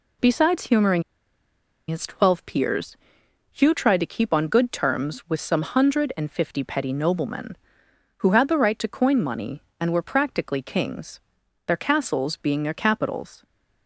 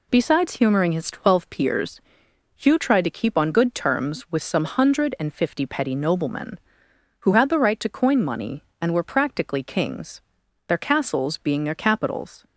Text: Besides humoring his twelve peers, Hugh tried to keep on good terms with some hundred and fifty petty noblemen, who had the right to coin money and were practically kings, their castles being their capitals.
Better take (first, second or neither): second